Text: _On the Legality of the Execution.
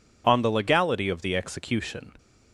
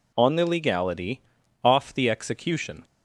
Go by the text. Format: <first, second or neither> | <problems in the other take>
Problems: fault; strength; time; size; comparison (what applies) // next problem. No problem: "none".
first | says "off" for "of"; at 1.6 s